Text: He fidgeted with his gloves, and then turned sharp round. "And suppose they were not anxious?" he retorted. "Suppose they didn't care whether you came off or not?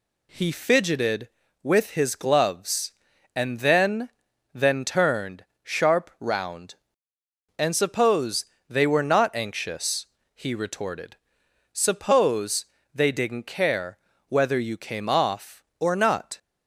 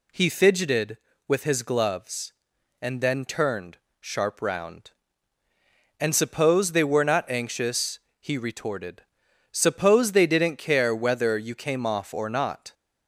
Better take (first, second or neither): second